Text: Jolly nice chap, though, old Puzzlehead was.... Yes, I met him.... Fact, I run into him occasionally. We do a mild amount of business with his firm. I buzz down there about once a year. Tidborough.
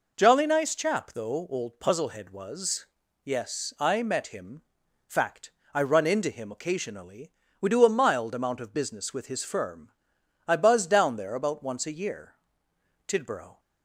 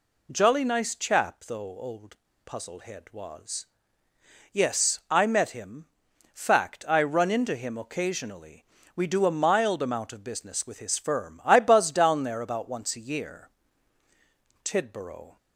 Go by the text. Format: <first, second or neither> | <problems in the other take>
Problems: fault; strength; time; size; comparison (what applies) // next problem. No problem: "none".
first | pauses between "old" and "Puzzlehead"; slight; at 2.1 s; 0.30 s long